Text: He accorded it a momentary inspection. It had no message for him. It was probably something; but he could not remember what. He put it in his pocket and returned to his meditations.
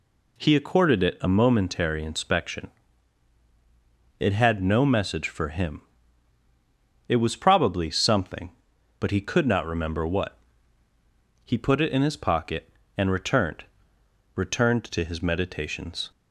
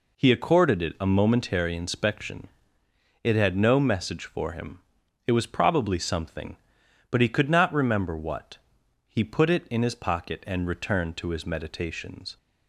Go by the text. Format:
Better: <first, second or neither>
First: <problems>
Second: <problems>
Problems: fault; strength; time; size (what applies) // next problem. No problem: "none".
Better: second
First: says "returned" twice; at 14.3 s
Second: none